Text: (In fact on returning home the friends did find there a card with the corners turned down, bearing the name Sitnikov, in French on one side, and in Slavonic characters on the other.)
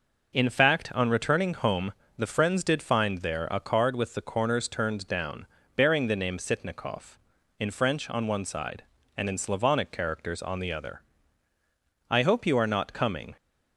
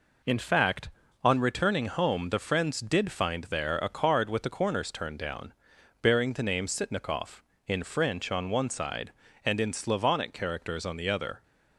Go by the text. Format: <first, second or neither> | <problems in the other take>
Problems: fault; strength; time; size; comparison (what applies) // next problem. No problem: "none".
second | pauses between "home" and "the"; slight; at 1.9 s; 0.26 s long // goes on to say "I hope you are not coming"; noticeable; from 12.0 s on; 1.2 s long